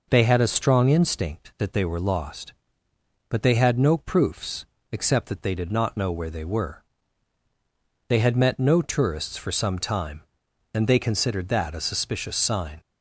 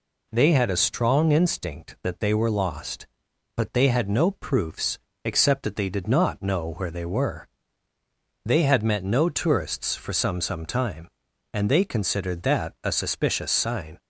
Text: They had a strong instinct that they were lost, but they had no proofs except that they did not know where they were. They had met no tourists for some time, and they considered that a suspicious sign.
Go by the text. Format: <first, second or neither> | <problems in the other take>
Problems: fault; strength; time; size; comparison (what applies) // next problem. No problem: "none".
first | pauses between "proofs" and "except"; slight; at 4.9 s; 0.26 s long; slight in the first // says "some" twice; at 10.4 s